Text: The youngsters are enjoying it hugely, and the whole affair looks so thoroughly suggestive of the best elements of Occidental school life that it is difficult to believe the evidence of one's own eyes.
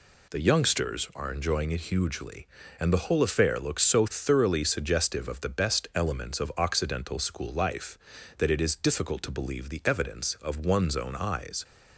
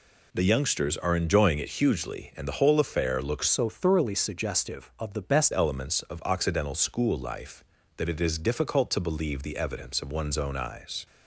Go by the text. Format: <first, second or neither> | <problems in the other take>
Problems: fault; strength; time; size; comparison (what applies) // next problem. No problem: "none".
first | changes voice from "so" to "best"; from 3.4 to 5.5 s; 2.1 s long